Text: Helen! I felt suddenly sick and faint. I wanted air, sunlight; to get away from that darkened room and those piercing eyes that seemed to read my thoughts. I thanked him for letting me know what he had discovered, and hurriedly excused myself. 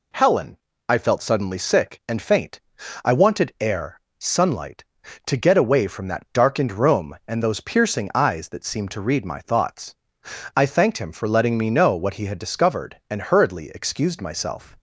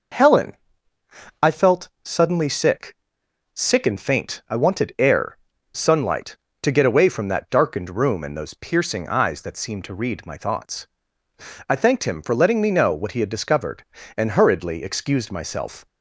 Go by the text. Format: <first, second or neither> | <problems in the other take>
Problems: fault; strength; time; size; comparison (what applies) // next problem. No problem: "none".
first | pauses between "felt" and "suddenly"; slight; at 1.8 s; 0.16 s long // says "sick" twice; at 3.5 s